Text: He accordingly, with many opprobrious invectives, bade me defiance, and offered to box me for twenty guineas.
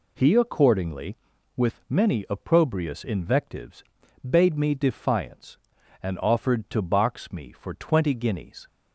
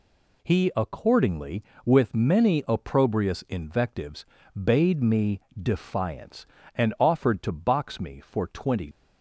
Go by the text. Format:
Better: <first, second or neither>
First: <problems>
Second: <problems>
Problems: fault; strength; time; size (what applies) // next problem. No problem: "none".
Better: first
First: none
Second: pauses between "me" and "defiance"; slight; at 5.4 s; 0.18 s long // stops before "guineas"; at 8.9 s